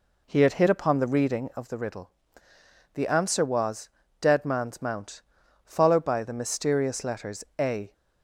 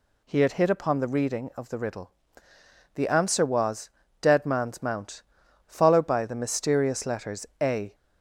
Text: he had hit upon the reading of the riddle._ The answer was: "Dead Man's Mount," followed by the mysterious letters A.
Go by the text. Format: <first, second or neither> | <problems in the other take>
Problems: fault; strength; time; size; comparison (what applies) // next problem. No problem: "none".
second | starts louder than the rest; slight; until 1.7 s; 3.5 dB // pauses between "letters" and "A"; slight; at 7.4 s; 0.16 s long; slight in the second